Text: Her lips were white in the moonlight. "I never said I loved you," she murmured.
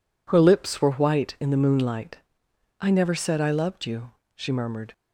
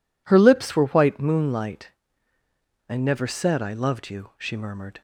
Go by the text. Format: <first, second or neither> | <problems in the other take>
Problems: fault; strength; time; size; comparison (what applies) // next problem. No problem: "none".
first | skips "in the"; at 1.1 s